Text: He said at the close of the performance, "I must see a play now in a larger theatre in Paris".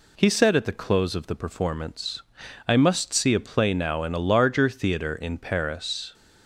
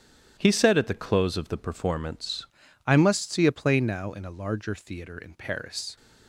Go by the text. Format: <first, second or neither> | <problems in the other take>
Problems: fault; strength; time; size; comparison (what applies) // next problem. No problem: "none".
first | starts louder than the rest; strong; until 1.4 s; 11 dB // changes voice at "I"; from 2.8 s on; 3.1 s long